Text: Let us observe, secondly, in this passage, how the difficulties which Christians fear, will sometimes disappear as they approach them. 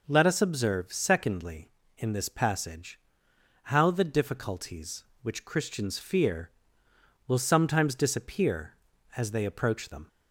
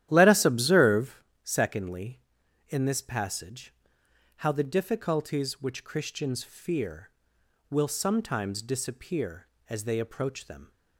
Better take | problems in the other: first | starts louder than the rest; strong; until 1.4 s; 11.5 dB

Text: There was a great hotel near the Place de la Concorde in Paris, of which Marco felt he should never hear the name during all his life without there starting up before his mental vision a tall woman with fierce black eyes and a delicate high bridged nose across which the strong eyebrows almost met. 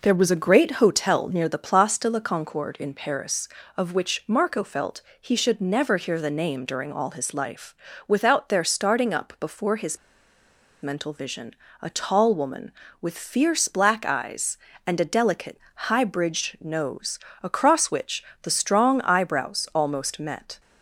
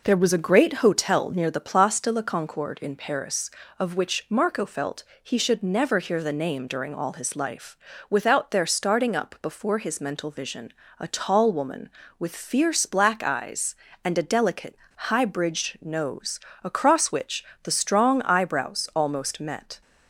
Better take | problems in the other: second | pauses between "felt" and "he"; slight; at 5.0 s; 0.18 s long; slight in the second // pauses between "life" and "without"; slight; at 7.7 s; 0.32 s long; slight in the second // pauses between "his" and "mental"; noticeable; at 9.9 s; 0.86 s long // pauses between "vision" and "a"; slight; at 11.5 s; 0.26 s long; slight in the second // pauses between "delicate" and "high"; slight; at 15.5 s; 0.32 s long; slight in the second // pauses between "nose" and "across"; slight; at 17.1 s; 0.24 s long; slight in the second // pauses between "which" and "the"; slight; at 18.2 s; 0.20 s long; slight in the second

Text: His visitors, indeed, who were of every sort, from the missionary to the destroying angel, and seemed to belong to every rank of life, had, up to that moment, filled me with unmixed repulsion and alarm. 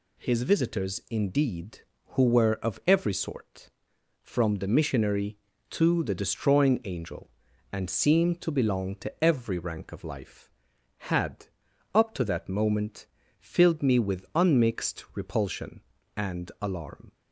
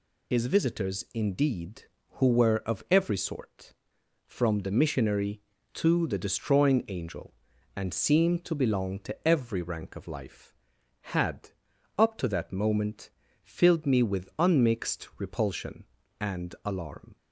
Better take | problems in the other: first | loses the start of "His"; at 0.3 s; 90 ms

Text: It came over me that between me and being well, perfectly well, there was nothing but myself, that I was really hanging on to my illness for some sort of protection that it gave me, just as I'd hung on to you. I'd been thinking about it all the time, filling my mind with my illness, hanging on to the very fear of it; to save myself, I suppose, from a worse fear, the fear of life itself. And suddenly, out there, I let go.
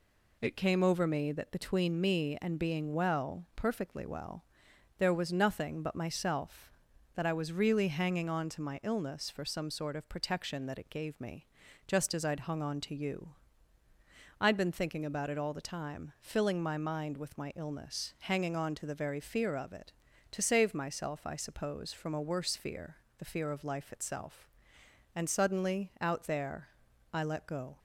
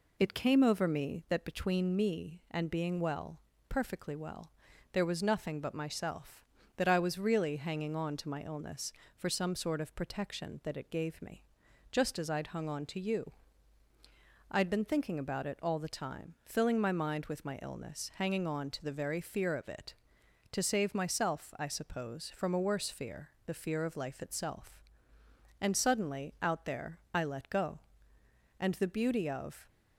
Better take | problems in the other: first | goes on to say "And the beauty of"; noticeable; from 28.5 s on; 1.1 s long

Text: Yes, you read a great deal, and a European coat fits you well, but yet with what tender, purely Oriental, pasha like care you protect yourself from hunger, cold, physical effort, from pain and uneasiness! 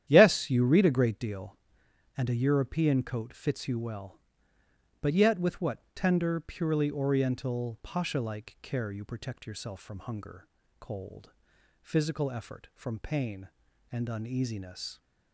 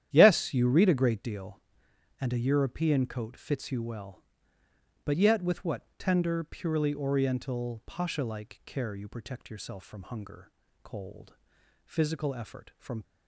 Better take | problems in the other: first | starts louder than the rest; strong; until 1.1 s; 10.5 dB; strong in the first // pauses between "what" and "tender"; slight; at 5.8 s; 0.16 s long; slight in the first // stops before "pain and uneasiness"; at 13.0 s

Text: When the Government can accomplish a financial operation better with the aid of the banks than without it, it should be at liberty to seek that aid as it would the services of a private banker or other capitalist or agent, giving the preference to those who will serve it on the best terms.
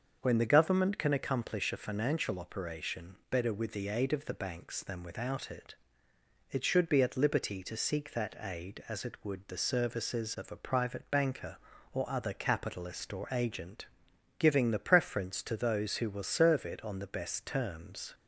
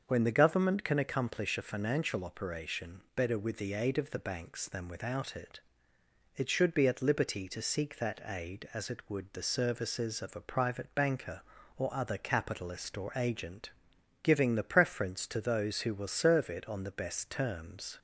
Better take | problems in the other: neither | starts louder than the rest; the same in both

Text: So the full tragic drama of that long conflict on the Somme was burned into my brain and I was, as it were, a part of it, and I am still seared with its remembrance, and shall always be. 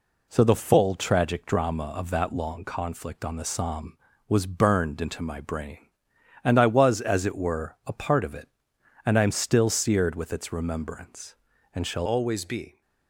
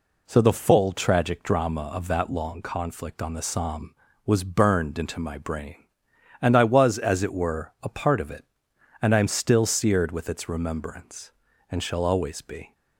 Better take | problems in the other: second | changes voice at "always"; from 12.0 s on; 0.8 s long

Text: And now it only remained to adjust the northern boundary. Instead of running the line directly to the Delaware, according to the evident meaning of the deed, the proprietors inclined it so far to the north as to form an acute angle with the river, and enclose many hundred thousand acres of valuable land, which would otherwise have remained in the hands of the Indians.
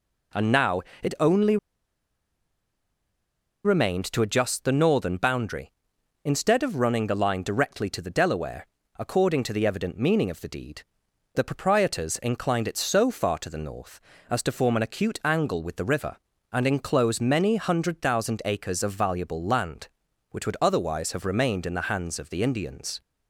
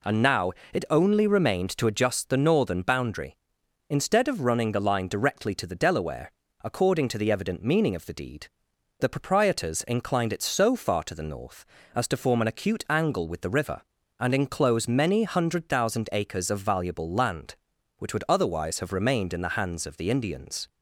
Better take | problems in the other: second | pauses between "now" and "it"; slight; at 0.8 s; 0.22 s long; slight in the second // pauses between "only" and "remained"; strong; at 1.5 s; 2.0 s long

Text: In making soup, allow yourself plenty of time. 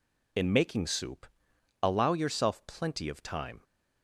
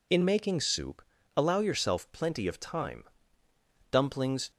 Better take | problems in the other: first | goes on to say "Dumplings"; from 3.9 s on; 0.60 s long

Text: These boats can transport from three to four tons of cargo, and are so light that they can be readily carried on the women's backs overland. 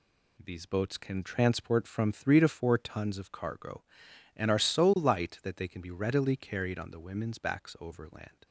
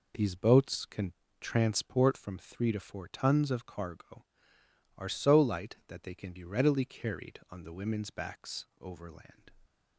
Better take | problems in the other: first | pauses between "can" and "transport"; slight; at 1.1 s; 0.30 s long // skips "and"; at 4.6 s

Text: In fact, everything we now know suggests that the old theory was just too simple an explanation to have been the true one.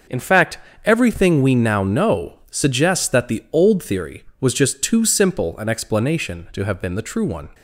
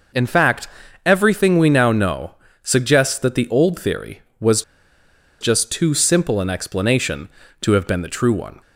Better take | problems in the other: first | pauses between "know" and "suggests"; slight; at 2.3 s; 0.26 s long // pauses between "was" and "just"; noticeable; at 4.6 s; 0.79 s long

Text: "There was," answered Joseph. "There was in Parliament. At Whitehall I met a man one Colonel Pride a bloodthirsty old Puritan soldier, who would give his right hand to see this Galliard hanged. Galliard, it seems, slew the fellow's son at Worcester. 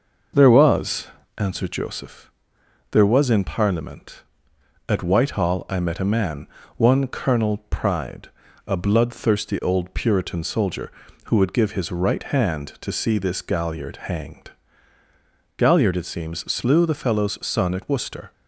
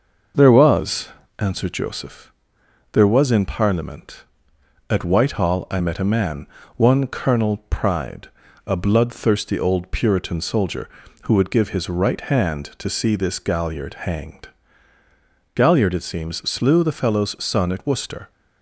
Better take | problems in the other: neither | pauses between "man" and "one"; slight; the same in both // pauses between "Pride" and "a"; slight; the same in both

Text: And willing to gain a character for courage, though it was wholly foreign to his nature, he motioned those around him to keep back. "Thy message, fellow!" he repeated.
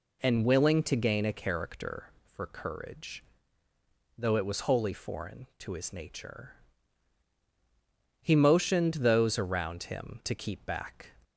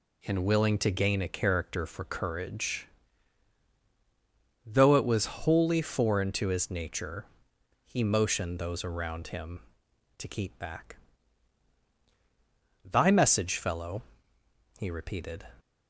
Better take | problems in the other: second | stops before "Thy message fellow he repeated"; at 11.2 s

